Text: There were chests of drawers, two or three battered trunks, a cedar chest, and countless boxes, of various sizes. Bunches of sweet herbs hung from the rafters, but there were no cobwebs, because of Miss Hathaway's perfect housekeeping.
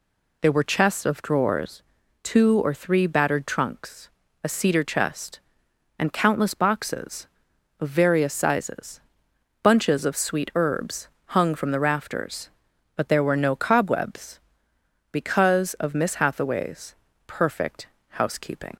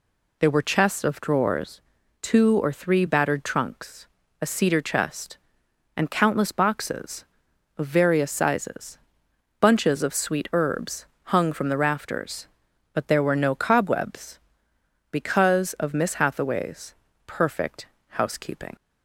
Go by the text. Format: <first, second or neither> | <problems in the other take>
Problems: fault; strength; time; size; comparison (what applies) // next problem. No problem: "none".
neither | pauses between "herbs" and "hung"; slight; the same in both // pauses between "Hathaway's" and "perfect"; slight; the same in both // pauses between "perfect" and "housekeeping"; slight; the same in both